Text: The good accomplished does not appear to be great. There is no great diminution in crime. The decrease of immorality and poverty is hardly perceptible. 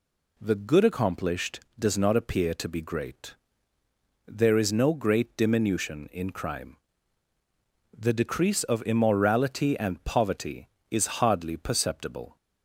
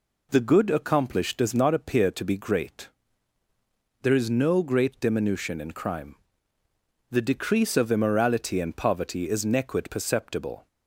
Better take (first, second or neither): first